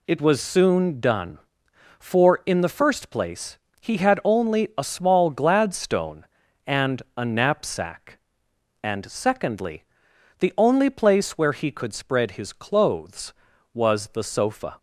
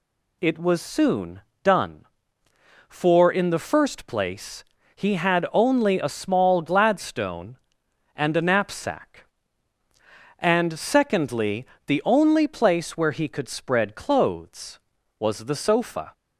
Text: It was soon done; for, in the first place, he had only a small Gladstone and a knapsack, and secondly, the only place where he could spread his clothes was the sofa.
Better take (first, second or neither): first